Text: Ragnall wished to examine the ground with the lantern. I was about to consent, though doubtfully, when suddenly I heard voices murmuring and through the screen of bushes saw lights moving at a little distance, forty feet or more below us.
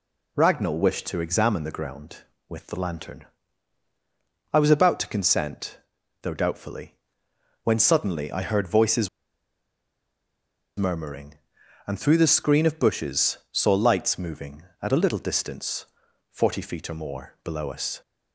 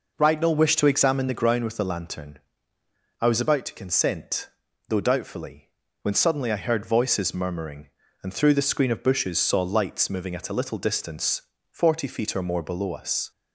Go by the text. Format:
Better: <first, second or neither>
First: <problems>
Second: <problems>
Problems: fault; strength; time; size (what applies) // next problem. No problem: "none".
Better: second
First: pauses between "voices" and "murmuring"; strong; at 9.0 s; 1.6 s long // pauses between "bushes" and "saw"; slight; at 13.3 s; 0.16 s long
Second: none